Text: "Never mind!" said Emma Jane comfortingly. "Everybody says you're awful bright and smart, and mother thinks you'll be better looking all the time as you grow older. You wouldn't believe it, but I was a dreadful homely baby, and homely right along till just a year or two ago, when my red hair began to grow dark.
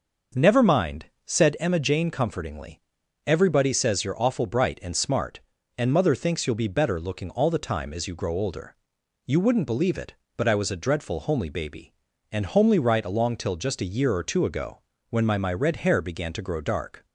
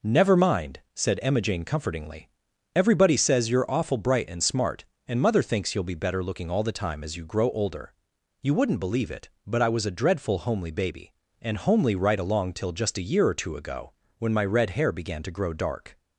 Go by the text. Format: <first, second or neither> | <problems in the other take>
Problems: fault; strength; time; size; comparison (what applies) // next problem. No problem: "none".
second | starts louder than the rest; noticeable; until 1.6 s; 6 dB // says "my" twice; at 15.3 s